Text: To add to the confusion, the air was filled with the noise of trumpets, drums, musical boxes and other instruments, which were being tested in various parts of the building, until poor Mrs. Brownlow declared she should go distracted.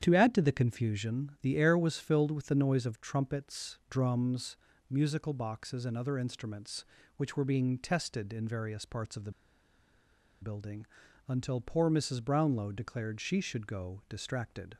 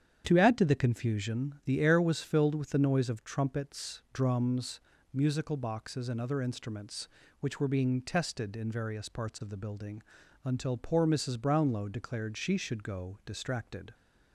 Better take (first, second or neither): second